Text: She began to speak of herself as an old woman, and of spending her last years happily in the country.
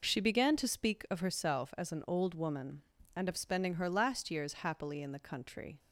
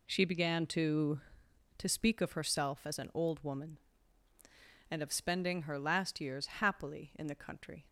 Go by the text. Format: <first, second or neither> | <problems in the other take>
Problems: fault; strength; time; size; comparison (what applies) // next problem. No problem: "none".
first | says "to" twice; at 1.7 s